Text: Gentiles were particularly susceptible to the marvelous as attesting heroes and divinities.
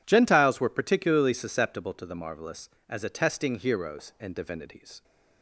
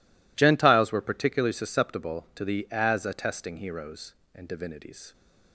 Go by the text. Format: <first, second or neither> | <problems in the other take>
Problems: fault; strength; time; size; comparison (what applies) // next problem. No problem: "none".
first | skips "marvelous"; at 2.6 s